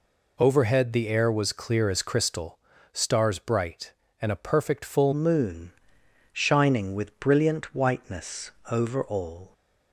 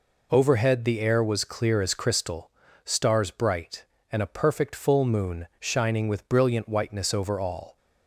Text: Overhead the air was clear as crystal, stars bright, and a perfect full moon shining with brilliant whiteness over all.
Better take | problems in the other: second | changes voice at "moon"; from 5.1 s on; 4.4 s long // pauses between "moon" and "shining"; noticeable; at 5.7 s; 0.62 s long // pauses between "whiteness" and "over"; slight; at 8.5 s; 0.18 s long

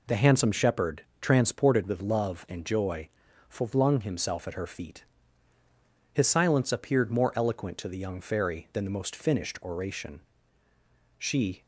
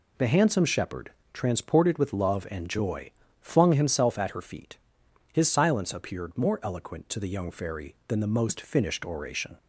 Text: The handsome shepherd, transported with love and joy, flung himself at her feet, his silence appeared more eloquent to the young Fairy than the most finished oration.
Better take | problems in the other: second | goes on to say "She"; slight; from 11.1 s on; 0.48 s long

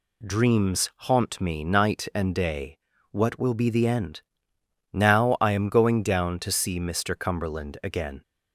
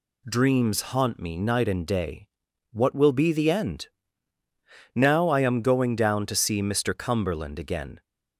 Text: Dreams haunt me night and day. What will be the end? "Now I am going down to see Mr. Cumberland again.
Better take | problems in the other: neither | none

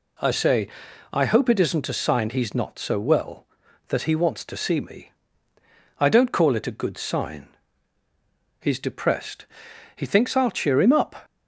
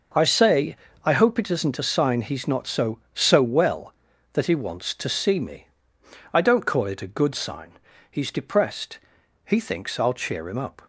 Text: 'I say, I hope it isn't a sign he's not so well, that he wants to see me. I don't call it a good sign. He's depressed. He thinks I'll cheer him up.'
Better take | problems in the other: first | says "so" twice; at 3.1 s

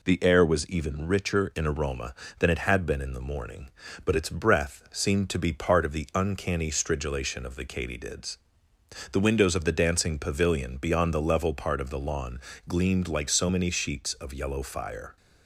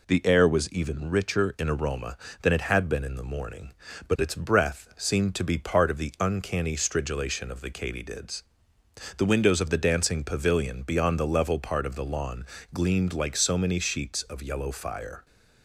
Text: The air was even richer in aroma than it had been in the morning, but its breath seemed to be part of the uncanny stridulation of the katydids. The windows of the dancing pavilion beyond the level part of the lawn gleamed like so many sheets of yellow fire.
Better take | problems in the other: neither | pauses between "lawn" and "gleamed"; slight; the same in both

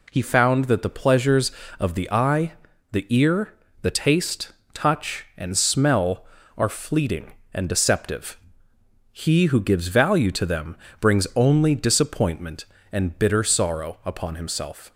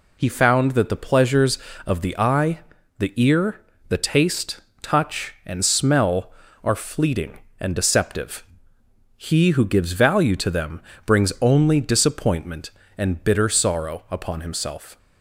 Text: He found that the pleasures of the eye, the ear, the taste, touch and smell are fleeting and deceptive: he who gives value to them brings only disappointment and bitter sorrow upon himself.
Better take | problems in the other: first | loses the start of "He"; at 0.1 s; 35 ms // pauses between "them" and "brings"; slight; at 10.8 s; 0.24 s long; slight in the first

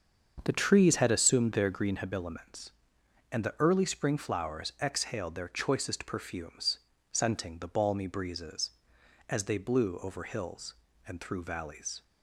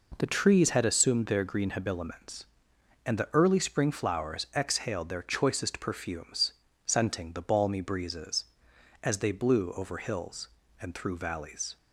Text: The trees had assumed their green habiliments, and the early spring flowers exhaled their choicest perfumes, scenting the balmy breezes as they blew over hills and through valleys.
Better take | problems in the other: second | starts louder than the rest; until 2.1 s; 7 dB

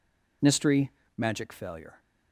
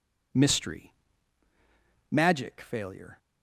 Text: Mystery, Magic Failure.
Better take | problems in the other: neither | none

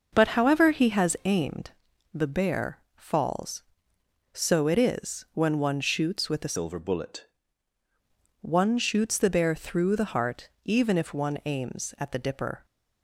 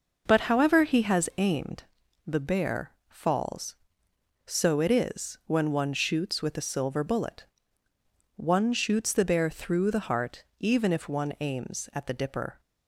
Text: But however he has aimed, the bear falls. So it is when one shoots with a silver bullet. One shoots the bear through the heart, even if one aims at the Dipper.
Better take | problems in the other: second | pauses between "bear" and "falls"; slight; at 2.7 s; 0.16 s long; slight in the second // changes voice from "silver" to "bullet"; from 6.5 to 7.2 s; 0.7 s long

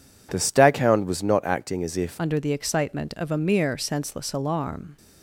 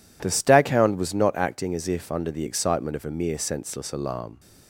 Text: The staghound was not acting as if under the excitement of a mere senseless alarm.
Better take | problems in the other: second | changes voice at "under"; from 2.1 s on; 2.8 s long

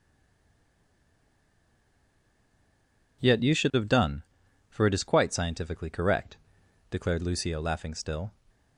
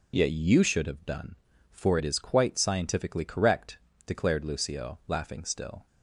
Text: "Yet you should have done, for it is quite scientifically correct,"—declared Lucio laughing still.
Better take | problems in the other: second | stays silent before the first word; strong; until 3.2 s; 3.2 s long

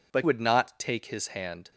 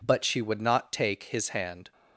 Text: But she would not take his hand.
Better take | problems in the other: second | skips "she"; at 0.2 s

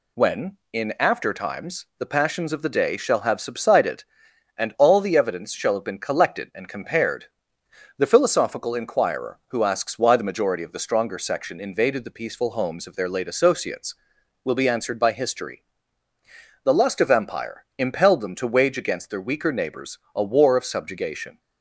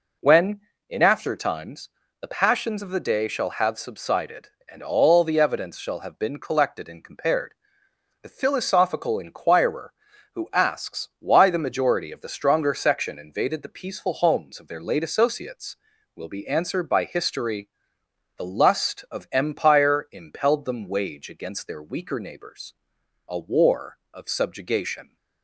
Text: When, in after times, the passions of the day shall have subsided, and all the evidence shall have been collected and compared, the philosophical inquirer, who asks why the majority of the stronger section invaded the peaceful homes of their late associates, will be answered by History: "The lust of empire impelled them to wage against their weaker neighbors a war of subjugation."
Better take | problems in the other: first | skips "to"; at 20.8 s // pauses between "neighbors" and "a"; noticeable; at 22.7 s; 0.52 s long; slight in the first

